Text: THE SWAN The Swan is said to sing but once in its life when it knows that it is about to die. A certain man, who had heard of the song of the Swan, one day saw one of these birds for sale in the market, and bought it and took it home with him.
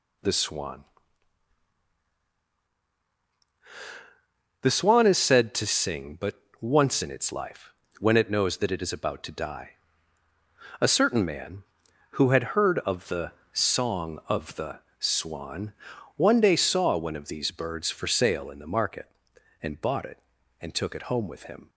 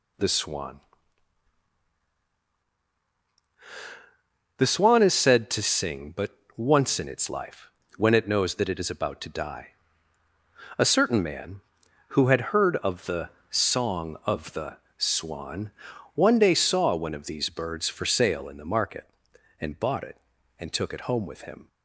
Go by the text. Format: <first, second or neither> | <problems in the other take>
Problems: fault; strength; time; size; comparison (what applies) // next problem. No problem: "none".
neither | pauses between "SWAN" and "The"; strong; the same in both // pauses between "but" and "once"; slight; the same in both // pauses between "life" and "when"; slight; the same in both // pauses between "the" and "song"; slight; the same in both // pauses between "the" and "Swan"; slight; the same in both